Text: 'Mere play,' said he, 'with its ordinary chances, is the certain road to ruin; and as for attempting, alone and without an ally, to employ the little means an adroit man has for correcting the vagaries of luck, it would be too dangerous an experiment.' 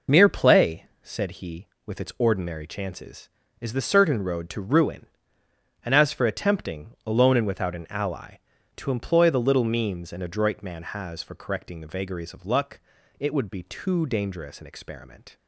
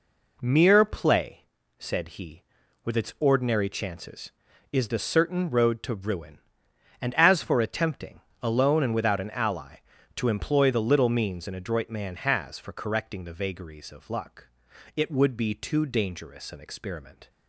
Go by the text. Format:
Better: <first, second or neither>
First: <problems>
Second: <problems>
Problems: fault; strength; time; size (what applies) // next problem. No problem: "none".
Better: second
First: loses the start of "Mere"; at 0.0 s; 25 ms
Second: none